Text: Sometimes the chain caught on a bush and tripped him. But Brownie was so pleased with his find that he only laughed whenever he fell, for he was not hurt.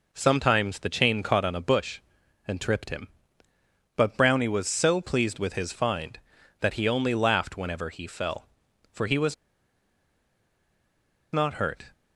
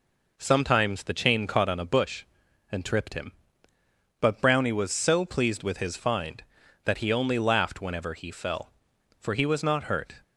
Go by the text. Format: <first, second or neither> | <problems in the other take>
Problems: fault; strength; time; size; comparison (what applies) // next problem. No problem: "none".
second | pauses between "was" and "not"; strong; at 9.3 s; 1.9 s long